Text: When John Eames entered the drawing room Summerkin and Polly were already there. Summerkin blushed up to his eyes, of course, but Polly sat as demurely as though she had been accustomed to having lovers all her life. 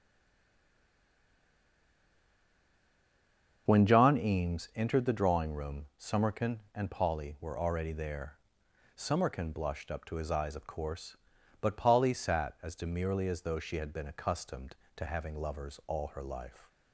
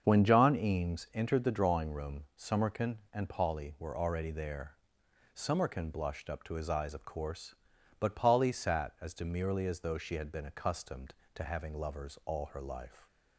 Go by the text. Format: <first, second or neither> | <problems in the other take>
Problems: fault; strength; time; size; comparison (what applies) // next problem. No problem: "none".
second | stays silent before the first word; strong; until 3.6 s; 3.6 s long // starts louder than the rest; until 4.6 s; 7 dB; also in the second